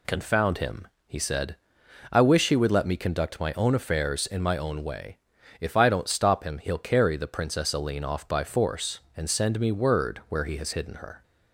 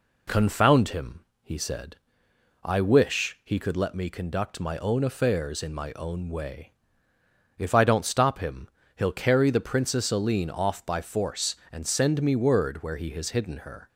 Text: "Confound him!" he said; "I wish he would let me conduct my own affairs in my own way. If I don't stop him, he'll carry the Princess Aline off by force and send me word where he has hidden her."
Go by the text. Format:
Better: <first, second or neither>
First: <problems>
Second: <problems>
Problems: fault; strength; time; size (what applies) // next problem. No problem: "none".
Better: first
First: none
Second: says "could" for "would"; at 3.5 s